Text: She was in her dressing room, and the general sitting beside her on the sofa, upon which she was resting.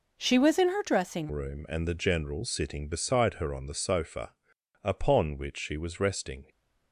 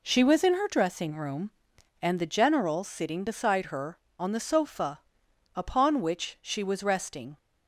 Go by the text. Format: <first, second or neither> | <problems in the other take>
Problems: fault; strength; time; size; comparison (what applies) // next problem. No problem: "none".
second | changes voice at "room"; from 1.3 s on; 5.1 s long